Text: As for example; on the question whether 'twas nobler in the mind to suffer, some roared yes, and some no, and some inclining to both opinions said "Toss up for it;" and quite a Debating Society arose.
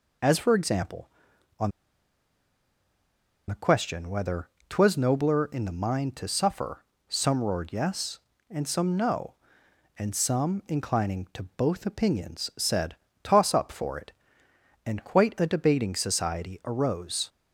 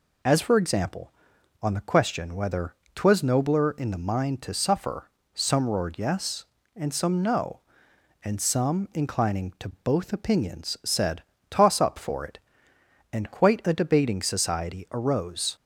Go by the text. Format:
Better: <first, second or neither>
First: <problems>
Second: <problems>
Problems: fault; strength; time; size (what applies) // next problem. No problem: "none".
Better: second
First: pauses between "on" and "the"; strong; at 1.7 s; 1.7 s long // pauses between "whether" and "twas"; slight; at 4.4 s; 0.22 s long // pauses between "said" and "Toss"; slight; at 12.9 s; 0.26 s long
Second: pauses between "whether" and "twas"; slight; at 2.7 s; 0.22 s long // pauses between "said" and "Toss"; slight; at 11.2 s; 0.26 s long